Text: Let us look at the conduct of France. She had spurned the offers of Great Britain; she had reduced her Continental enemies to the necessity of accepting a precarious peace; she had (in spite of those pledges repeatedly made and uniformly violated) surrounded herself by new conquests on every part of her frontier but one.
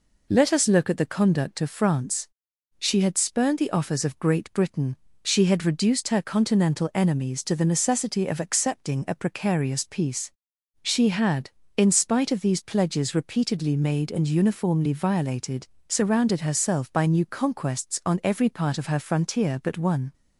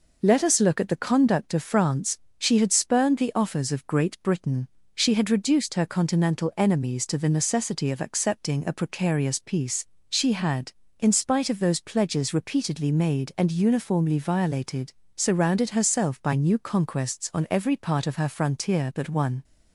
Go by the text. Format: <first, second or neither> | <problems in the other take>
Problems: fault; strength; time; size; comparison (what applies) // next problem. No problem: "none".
second | says "these" for "those"; at 12.3 s